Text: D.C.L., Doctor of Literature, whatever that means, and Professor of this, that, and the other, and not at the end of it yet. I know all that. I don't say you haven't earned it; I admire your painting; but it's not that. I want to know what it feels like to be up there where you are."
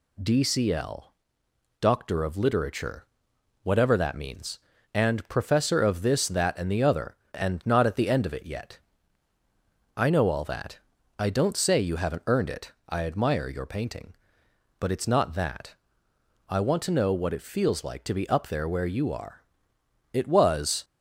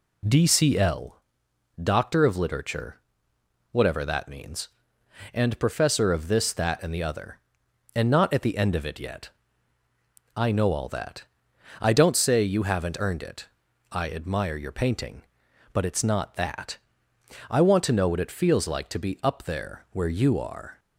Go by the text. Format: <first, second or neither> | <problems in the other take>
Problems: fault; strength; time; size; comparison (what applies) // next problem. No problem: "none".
second | goes on to say "It was"; noticeable; from 20.1 s on; 0.72 s long